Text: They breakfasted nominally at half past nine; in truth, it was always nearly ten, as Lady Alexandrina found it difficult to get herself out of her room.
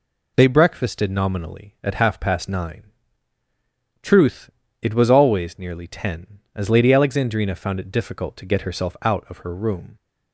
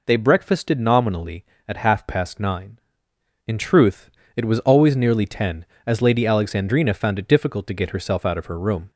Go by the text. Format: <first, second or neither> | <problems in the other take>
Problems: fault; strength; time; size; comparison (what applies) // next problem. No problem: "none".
second | skips "in"; at 3.4 s